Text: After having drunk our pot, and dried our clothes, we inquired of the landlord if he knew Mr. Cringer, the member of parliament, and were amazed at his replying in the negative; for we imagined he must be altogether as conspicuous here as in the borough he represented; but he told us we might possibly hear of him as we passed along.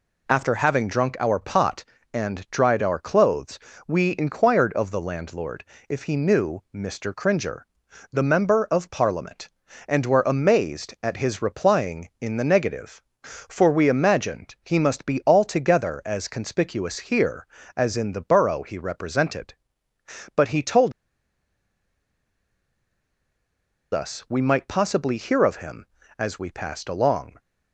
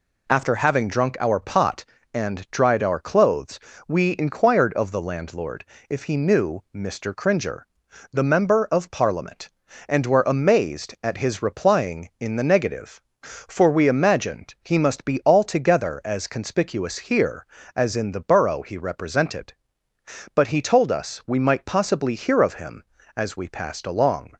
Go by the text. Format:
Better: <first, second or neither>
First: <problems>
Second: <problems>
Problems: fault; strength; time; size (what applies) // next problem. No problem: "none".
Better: second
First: pauses between "landlord" and "if"; slight; at 5.6 s; 0.24 s long // pauses between "told" and "us"; strong; at 20.9 s; 3.0 s long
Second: pauses between "landlord" and "if"; slight; at 5.6 s; 0.24 s long